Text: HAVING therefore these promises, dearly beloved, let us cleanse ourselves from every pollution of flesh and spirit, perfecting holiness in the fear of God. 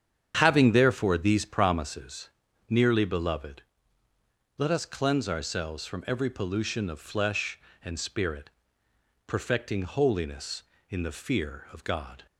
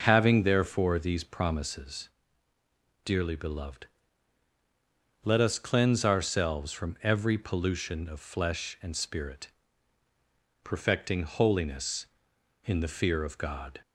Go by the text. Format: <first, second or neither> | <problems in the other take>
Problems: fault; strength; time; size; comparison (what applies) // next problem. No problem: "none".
second | starts louder than the rest; strong; until 1.4 s; 8.5 dB // says "nearly" for "dearly"; at 2.6 s